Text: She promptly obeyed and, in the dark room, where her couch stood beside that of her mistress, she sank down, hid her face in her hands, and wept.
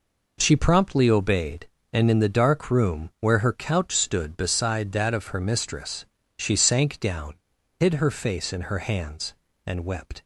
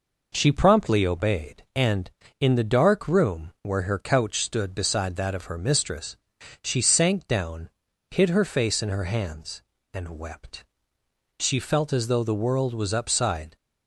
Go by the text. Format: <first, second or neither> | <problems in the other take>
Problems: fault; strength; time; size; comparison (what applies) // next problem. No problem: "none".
first | goes on to say "She felt as though the world was upside"; strong; from 11.3 s on; 2.1 s long